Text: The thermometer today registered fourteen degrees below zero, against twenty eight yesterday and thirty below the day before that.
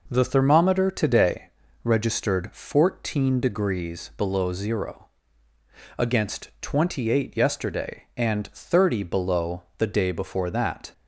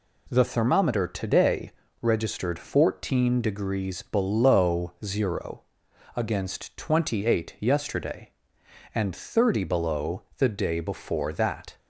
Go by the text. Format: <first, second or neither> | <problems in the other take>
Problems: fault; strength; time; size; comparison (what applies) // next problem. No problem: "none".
neither | pauses between "today" and "registered"; slight; the same in both